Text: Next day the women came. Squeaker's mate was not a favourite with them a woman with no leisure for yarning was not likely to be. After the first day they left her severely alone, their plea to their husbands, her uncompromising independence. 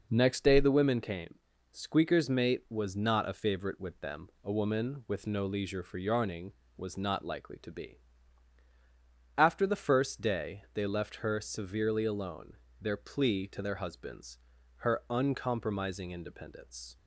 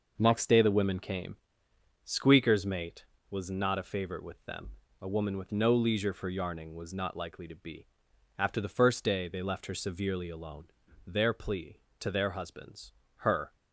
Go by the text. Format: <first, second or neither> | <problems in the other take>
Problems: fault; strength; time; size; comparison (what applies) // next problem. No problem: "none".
first | pauses between "them" and "a"; slight; at 4.7 s; 0.30 s long // stops before "uncompromising independence"; at 13.5 s